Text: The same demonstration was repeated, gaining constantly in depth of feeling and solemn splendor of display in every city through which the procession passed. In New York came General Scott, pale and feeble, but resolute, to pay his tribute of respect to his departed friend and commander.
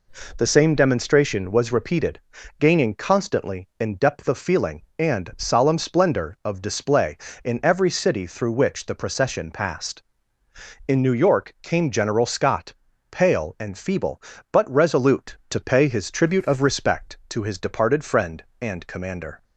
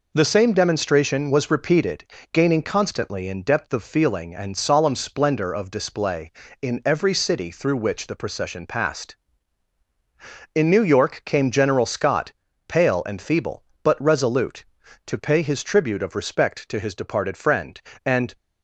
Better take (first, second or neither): first